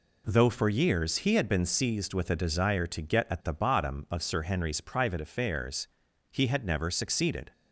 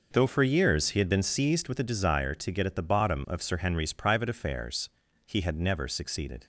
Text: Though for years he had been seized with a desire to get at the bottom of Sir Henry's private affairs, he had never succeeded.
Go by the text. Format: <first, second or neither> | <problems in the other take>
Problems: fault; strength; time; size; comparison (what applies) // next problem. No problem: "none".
neither | none